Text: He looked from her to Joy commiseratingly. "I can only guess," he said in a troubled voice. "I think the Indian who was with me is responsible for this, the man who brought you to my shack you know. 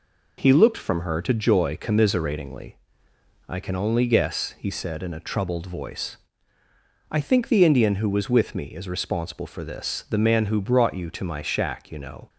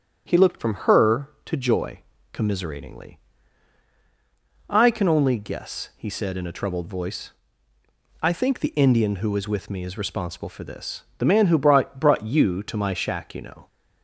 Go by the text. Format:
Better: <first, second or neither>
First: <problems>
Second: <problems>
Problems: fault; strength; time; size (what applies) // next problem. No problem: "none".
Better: first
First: none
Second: starts louder than the rest; strong; until 1.2 s; 7.5 dB // pauses between "Joy" and "commiseratingly"; slight; at 2.0 s; 0.32 s long // says "brought" twice; at 12.0 s